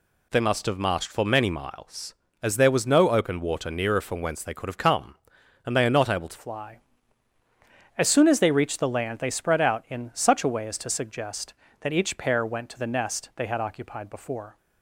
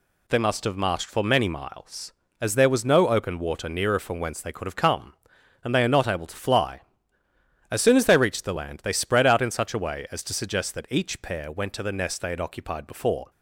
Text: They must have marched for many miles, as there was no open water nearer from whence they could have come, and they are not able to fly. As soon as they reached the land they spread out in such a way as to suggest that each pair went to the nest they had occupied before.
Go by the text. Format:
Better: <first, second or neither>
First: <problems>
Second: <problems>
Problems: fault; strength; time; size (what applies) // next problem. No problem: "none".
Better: second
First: changes voice at "fly"; from 6.3 s on; 8.2 s long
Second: none